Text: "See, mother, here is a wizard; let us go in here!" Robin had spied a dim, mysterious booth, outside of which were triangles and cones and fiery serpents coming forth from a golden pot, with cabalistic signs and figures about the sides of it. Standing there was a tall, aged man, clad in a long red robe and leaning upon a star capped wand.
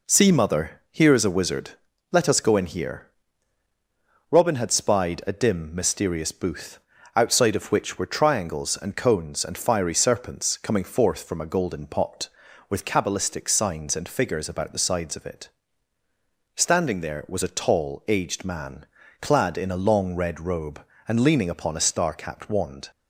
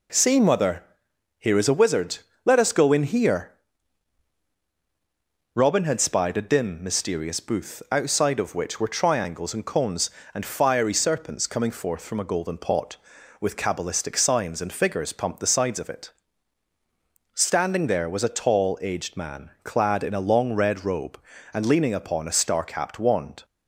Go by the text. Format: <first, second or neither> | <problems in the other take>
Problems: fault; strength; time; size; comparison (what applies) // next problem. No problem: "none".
first | says "pumped" for "about"; at 15.1 s